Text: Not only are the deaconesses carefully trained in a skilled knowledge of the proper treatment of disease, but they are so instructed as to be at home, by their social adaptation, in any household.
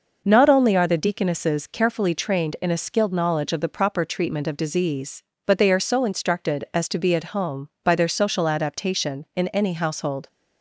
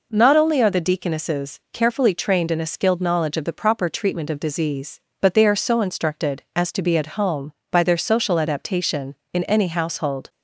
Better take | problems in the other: neither | none

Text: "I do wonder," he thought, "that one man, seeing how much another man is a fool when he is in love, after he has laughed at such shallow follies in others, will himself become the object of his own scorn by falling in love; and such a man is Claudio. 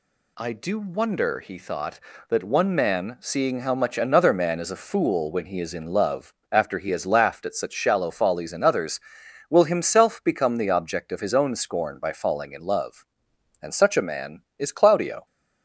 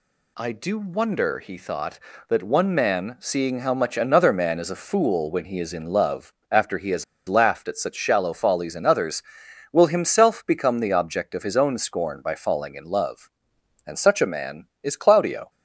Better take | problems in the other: first | pauses between "has" and "laughed"; slight; at 7.0 s; 0.23 s long

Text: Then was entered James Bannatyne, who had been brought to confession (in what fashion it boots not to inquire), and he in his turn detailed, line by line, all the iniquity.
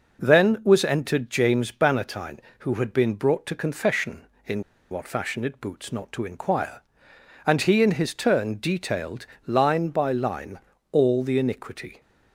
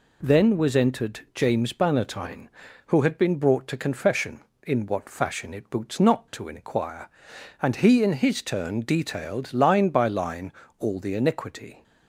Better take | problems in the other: second | pauses between "in" and "what"; slight; at 4.6 s; 0.28 s long

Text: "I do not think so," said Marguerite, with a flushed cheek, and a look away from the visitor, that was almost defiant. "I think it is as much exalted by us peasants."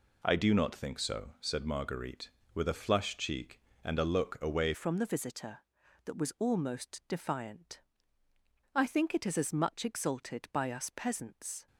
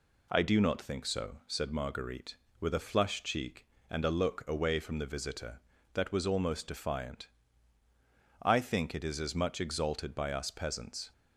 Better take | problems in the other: second | changes voice at "from"; from 4.7 s on; 6.9 s long

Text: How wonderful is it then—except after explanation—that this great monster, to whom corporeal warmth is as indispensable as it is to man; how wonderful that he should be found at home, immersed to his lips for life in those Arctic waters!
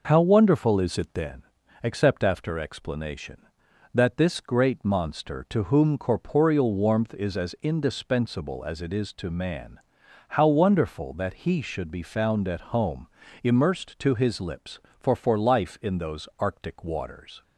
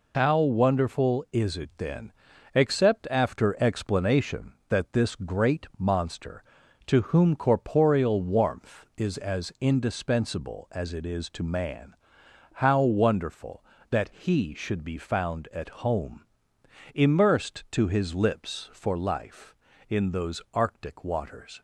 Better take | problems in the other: second | says "for" twice; at 15.1 s

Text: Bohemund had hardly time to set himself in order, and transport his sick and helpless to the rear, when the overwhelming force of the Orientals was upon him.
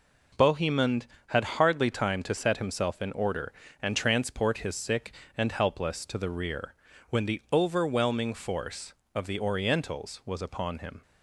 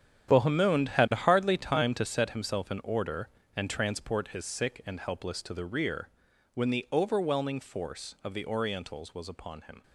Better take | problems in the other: first | gets quieter; strong; throughout; 12.5 dB

